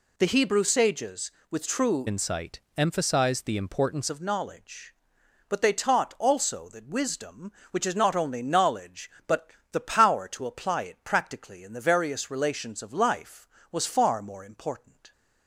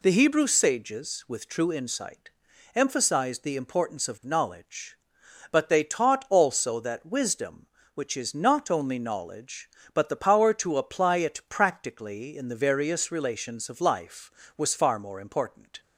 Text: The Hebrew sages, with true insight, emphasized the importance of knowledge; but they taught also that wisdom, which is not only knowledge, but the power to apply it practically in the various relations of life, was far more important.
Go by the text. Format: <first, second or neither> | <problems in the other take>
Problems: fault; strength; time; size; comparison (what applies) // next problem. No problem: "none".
second | changes voice from "insight" to "importance"; from 2.0 to 4.0 s; 2.0 s long // pauses between "but" and "the"; slight; at 9.5 s; 0.20 s long